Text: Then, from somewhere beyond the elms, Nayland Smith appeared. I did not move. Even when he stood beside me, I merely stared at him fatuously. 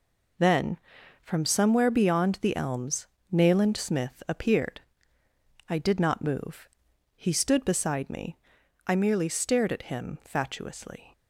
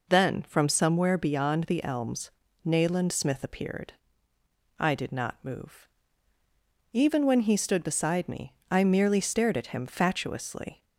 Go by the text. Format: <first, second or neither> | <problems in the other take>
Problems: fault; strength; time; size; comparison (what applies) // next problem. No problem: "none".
second | skips "Even when"; at 6.9 s